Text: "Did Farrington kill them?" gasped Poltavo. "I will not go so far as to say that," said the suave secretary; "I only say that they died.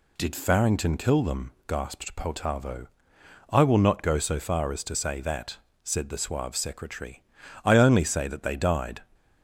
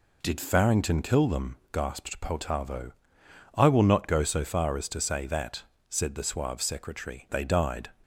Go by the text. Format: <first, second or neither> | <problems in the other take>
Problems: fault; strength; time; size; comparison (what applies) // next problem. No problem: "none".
first | skips "I only say that"; at 7.2 s